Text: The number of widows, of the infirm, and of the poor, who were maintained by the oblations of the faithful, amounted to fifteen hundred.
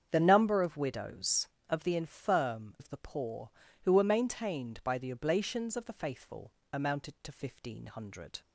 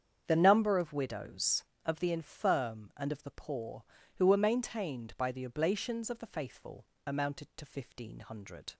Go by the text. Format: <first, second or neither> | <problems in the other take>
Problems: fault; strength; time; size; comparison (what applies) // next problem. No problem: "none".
second | starts louder than the rest; strong; until 1.1 s; 8 dB; strong in the second // skips "and"; at 2.7 s